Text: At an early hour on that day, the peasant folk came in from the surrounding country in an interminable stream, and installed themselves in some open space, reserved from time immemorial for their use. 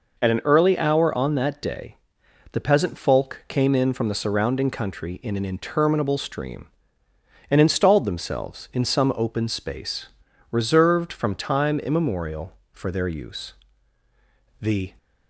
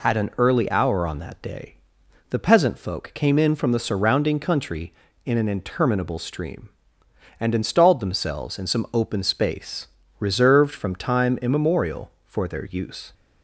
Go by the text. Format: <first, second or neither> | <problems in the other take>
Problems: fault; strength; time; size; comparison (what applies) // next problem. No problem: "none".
second | goes on to say "The"; slight; from 14.5 s on; 0.38 s long